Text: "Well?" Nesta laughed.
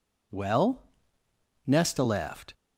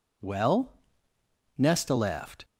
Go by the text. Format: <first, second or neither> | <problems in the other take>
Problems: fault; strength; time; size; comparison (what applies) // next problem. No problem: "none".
neither | none